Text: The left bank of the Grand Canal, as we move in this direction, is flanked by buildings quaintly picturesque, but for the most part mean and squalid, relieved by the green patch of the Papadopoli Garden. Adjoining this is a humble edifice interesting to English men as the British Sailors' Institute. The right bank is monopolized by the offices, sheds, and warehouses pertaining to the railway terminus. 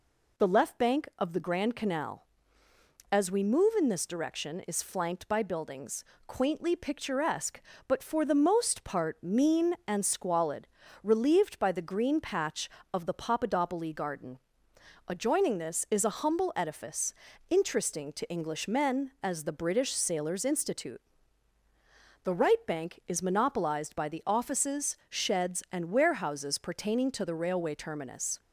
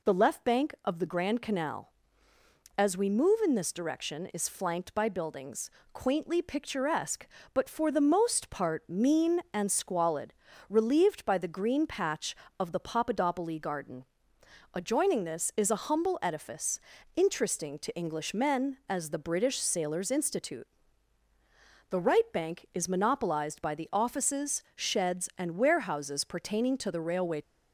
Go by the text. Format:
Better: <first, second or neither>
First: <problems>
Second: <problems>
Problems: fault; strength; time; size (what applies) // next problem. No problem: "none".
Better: first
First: pauses between "buildings" and "quaintly"; slight; at 6.0 s; 0.22 s long // pauses between "edifice" and "interesting"; slight; at 17.1 s; 0.34 s long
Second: pauses between "buildings" and "quaintly"; slight; at 5.7 s; 0.22 s long // pauses between "edifice" and "interesting"; slight; at 16.8 s; 0.34 s long // stops before "terminus"; at 27.4 s